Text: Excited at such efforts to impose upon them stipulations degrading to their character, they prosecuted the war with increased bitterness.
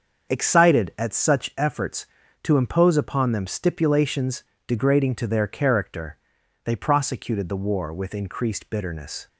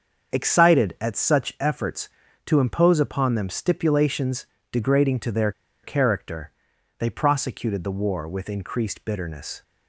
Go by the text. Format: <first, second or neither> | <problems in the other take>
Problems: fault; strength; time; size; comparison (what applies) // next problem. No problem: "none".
first | starts louder than the rest; until 1.3 s; 7 dB; also in the first // pauses between "stipulations" and "degrading"; slight; at 4.4 s; 0.26 s long; slight in the first // pauses between "their" and "character"; slight; at 5.5 s; 0.32 s long